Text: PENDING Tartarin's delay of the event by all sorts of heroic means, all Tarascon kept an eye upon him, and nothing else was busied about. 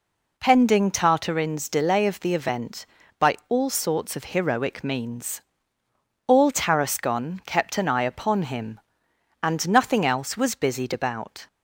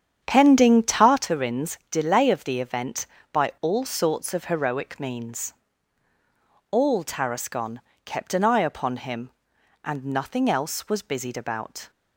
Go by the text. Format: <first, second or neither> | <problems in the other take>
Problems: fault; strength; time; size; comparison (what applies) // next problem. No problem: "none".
first | starts louder than the rest; strong; until 1.3 s; 8.5 dB // pauses between "Tarascon" and "kept"; slight; at 7.7 s; 0.24 s long